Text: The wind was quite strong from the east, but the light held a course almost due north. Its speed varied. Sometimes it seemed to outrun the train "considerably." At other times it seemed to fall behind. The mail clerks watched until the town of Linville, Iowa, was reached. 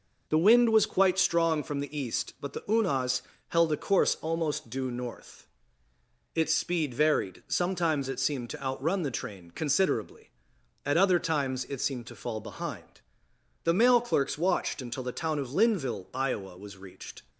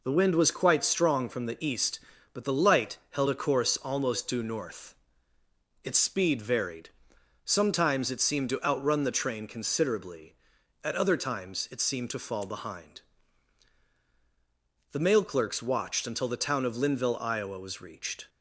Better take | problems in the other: second | says "unas" for "light"; at 2.6 s

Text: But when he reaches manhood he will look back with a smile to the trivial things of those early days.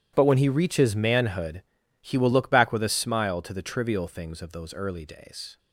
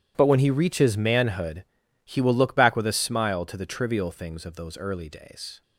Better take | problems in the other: neither | starts louder than the rest; strong; the same in both // pauses between "manhood" and "he"; the same in both

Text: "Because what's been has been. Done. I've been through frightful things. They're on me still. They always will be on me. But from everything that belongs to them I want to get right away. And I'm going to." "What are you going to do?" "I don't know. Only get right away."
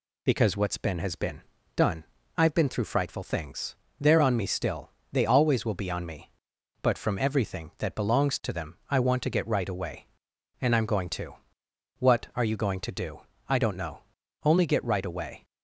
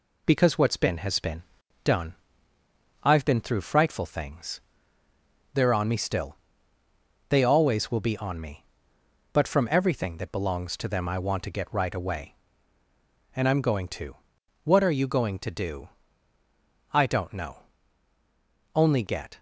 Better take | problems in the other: first | stops before "right away"; at 19.3 s

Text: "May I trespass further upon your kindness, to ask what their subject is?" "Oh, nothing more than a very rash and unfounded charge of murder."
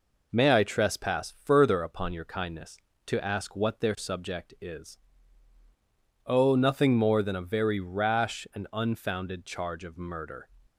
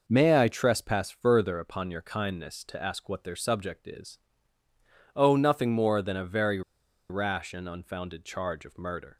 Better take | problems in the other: first | pauses between "very" and "rash"; noticeable; at 6.6 s; 0.49 s long

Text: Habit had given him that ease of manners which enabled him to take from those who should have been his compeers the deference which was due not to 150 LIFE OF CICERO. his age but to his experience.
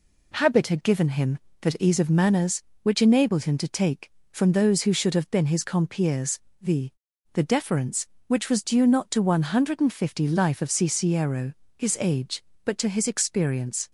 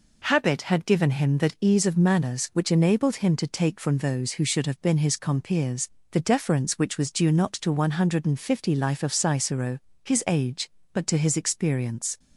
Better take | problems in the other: second | pauses between "compeers" and "the"; slight; at 6.3 s; 0.22 s long; slight in the second // says "the" twice; at 7.3 s

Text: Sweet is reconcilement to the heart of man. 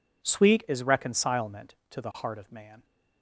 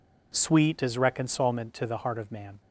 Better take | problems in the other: neither | none

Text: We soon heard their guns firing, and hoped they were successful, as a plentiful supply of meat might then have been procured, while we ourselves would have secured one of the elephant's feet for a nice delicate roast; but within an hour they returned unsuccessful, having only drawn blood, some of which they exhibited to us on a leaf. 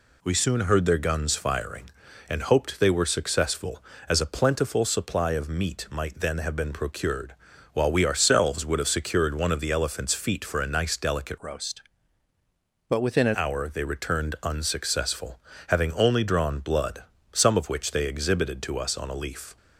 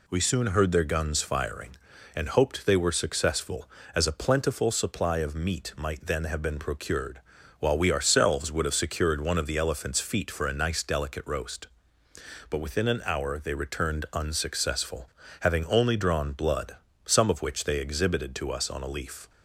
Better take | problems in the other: second | changes voice from "roast" to "an"; from 11.4 to 13.3 s; 1.9 s long

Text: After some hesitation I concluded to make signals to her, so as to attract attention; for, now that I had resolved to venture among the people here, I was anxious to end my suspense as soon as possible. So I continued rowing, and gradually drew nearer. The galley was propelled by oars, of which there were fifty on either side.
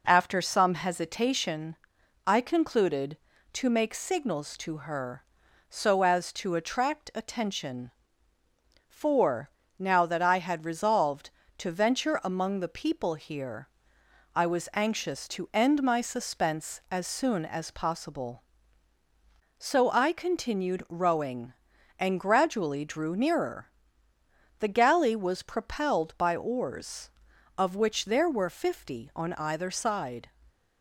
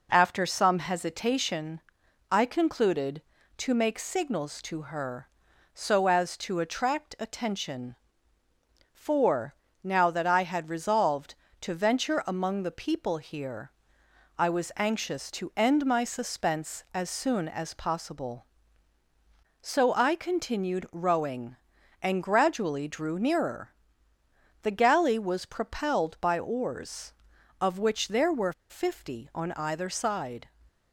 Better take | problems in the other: first | pauses between "hesitation" and "I"; noticeable; at 1.8 s; 0.52 s long; noticeable in the first // pauses between "were" and "fifty"; slight; at 28.5 s; 0.16 s long

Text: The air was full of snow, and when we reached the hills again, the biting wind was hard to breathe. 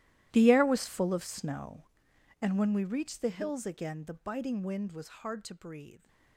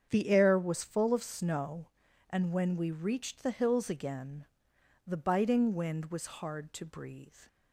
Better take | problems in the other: second | gets quieter; strong; throughout; 18.5 dB // starts louder than the rest; strong; until 1.3 s; 14 dB; strong in the second

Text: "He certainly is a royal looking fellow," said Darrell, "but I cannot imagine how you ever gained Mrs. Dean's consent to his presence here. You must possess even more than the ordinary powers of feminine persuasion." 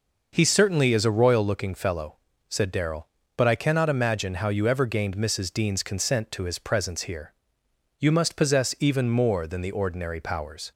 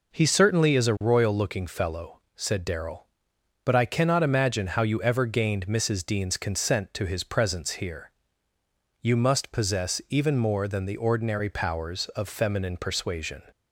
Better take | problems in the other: second | stops before "of feminine persuasion"; at 10.7 s

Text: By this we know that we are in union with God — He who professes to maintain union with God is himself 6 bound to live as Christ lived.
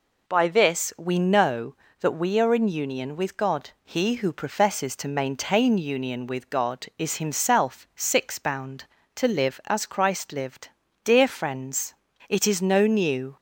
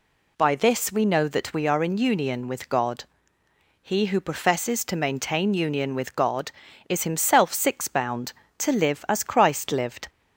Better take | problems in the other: second | goes on to say "Dear friends it is no new"; strong; from 11.0 s on; 2.3 s long

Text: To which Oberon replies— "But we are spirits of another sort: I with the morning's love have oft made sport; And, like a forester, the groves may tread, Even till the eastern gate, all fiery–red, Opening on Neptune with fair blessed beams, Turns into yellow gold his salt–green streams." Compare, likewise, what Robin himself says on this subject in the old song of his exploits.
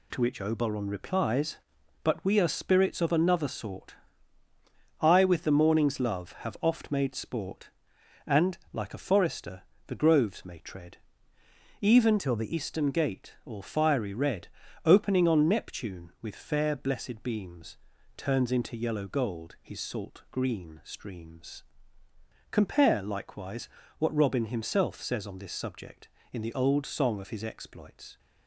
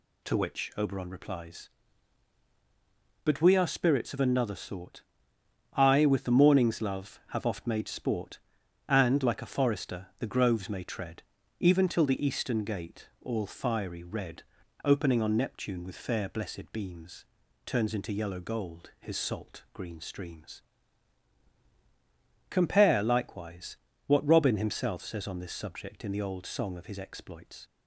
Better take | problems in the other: second | changes voice from "till" to "the"; from 12.1 to 12.5 s; 0.4 s long

